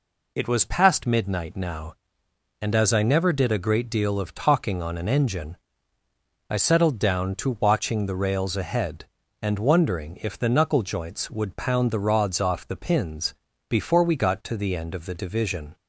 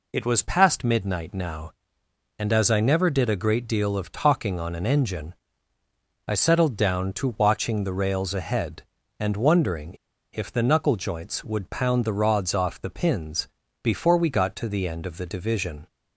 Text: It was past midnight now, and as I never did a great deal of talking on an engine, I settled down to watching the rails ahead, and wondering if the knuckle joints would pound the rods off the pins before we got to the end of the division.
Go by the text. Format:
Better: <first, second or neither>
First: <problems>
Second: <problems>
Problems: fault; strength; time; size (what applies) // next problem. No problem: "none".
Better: first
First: pauses between "pins" and "before"; slight; at 13.3 s; 0.34 s long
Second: pauses between "wondering" and "if"; at 9.9 s; 0.40 s long // pauses between "pins" and "before"; slight; at 13.4 s; 0.34 s long